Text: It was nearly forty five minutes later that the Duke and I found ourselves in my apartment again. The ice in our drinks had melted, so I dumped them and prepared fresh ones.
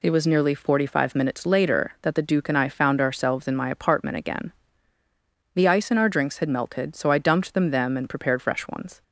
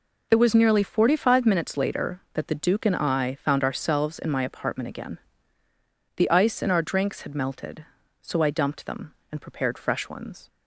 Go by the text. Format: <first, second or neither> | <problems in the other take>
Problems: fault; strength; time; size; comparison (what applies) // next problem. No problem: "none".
second | says "them" twice; at 7.7 s